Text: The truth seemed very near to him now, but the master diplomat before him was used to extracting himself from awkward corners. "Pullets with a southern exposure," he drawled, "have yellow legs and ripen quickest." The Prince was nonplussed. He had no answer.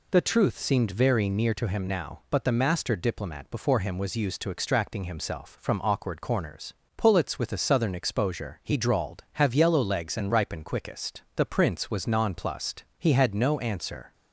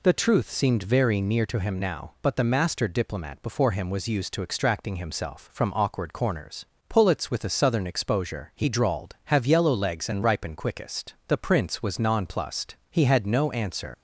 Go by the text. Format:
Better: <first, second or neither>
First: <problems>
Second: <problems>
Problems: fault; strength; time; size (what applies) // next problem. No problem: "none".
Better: first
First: none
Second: leaves "answer" unfinished; at 13.9 s; 100 ms